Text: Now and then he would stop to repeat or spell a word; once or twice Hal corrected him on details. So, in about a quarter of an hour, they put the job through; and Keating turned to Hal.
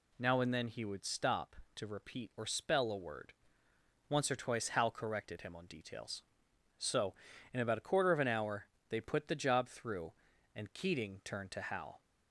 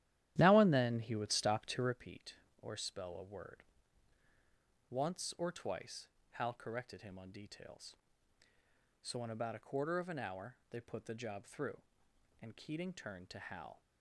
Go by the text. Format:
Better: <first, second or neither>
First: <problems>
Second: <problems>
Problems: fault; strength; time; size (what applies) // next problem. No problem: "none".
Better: first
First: none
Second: starts louder than the rest; strong; until 2.0 s; 12.5 dB // pauses between "twice" and "Hal"; slight; at 6.0 s; 0.24 s long